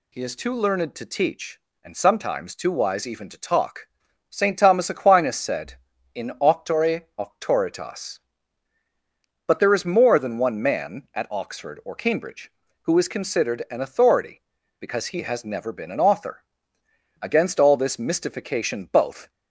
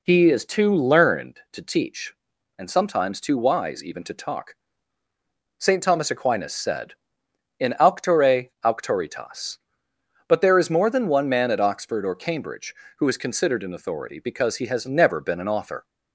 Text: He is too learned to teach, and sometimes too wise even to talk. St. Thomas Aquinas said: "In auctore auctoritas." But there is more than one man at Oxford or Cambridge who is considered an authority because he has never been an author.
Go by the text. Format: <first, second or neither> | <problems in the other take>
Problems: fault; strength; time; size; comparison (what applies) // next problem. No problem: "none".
second | goes on to say "Against all this mystification both"; strong; from 17.1 s on; 2.1 s long